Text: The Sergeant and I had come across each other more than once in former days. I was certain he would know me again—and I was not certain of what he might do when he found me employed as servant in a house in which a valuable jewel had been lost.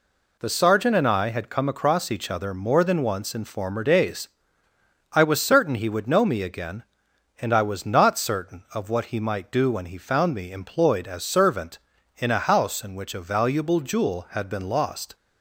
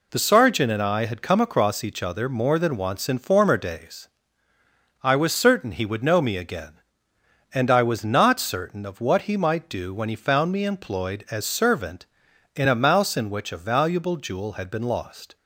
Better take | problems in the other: first | says "mouse" for "house"; at 12.7 s

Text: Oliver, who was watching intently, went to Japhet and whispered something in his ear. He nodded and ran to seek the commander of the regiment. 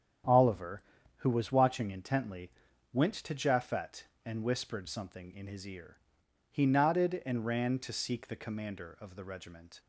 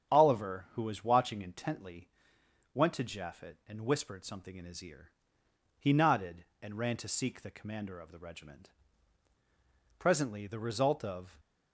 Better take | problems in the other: first | starts louder than the rest; strong; until 1.1 s; 9 dB; strong in the first // goes on to say "Presently the result of"; noticeable; from 10.1 s on; 1.2 s long

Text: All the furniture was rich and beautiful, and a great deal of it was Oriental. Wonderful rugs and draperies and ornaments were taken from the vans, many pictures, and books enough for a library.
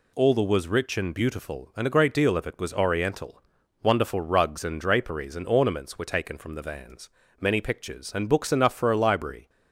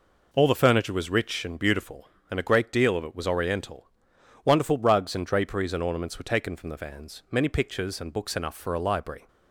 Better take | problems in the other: second | skips "furniture"; at 0.4 s

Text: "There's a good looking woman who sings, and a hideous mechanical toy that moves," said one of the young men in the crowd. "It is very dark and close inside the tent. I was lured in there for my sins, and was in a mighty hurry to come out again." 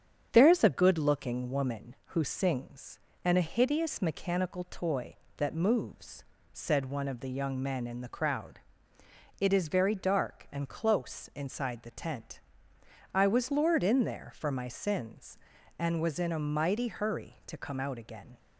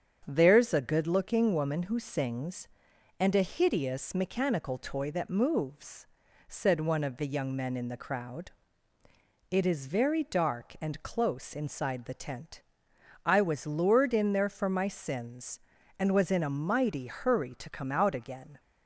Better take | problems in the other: neither | starts louder than the rest; strong; the same in both

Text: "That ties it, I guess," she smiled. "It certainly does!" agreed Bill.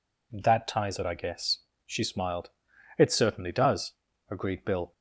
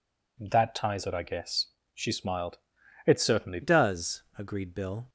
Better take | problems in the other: first | changes voice at "does"; from 3.6 s on; 1.4 s long

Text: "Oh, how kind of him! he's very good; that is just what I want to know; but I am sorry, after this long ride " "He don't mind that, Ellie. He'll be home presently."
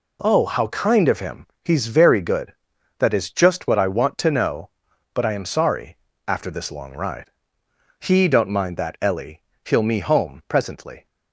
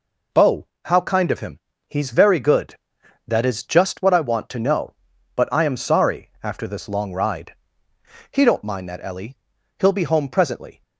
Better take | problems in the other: second | says "me" for "be"; at 9.8 s

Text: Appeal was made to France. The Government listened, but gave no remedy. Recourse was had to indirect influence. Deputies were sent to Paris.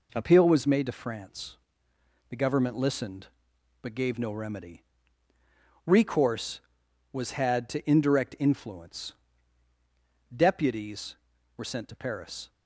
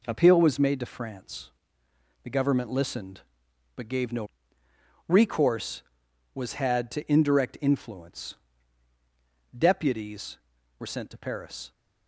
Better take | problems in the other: first | skips "remedy"; at 4.6 s

